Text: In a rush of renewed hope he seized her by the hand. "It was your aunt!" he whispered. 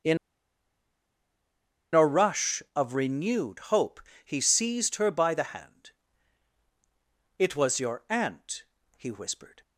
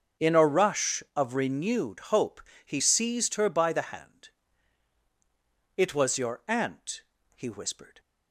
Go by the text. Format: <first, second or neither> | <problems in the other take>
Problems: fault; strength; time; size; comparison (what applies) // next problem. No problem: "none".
second | starts louder than the rest; until 2.9 s; 6.5 dB; also in the second // pauses between "In" and "a"; strong; at 0.1 s; 1.7 s long // pauses between "hope" and "he"; slight; at 4.0 s; 0.24 s long; slight in the second